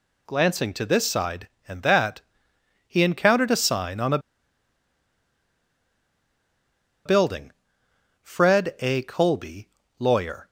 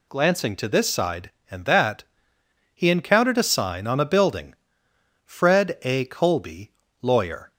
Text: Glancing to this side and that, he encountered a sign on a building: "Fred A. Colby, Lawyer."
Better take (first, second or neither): second